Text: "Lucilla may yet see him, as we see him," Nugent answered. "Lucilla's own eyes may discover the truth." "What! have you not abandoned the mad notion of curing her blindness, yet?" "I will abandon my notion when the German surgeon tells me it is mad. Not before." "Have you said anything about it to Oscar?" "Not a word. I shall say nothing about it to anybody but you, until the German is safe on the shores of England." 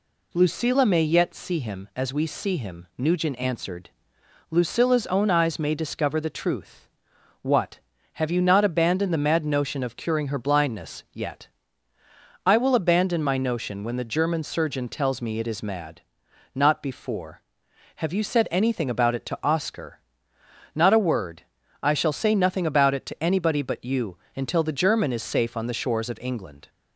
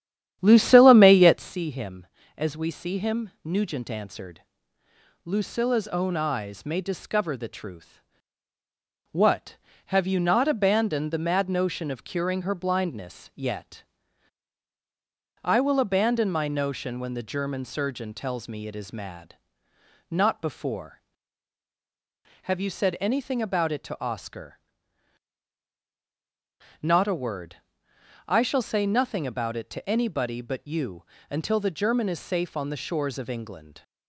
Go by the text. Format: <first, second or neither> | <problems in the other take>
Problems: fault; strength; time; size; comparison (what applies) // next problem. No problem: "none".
first | starts louder than the rest; strong; until 1.5 s; 10.5 dB